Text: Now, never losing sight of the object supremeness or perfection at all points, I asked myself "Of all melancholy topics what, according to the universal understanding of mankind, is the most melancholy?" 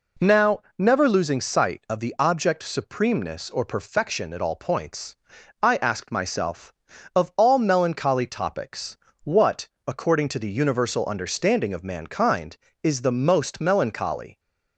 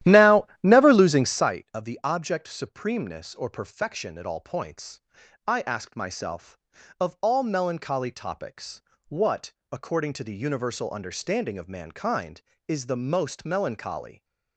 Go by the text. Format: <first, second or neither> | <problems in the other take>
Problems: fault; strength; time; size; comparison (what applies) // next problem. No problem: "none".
first | starts louder than the rest; strong; until 1.6 s; 13 dB // pauses between "topics" and "what"; slight; at 8.8 s; 0.26 s long; slight in the first